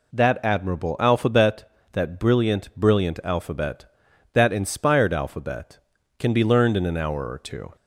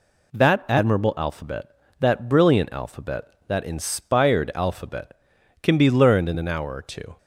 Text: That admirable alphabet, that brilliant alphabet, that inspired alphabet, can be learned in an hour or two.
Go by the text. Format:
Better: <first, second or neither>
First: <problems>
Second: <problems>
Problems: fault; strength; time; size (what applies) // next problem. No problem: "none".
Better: second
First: says "brilliant" twice; at 2.7 s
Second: none